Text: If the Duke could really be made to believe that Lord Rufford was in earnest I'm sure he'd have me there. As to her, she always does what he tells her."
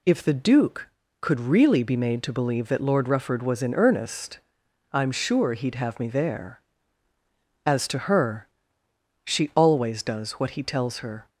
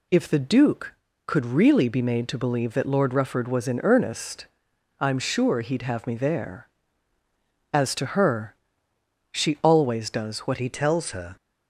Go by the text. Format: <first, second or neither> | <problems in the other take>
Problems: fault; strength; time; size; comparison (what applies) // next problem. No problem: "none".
first | pauses between "earnest" and "I'm"; noticeable; at 4.4 s; 0.54 s long; noticeable in the first // changes voice at "he"; from 10.5 s on; 0.8 s long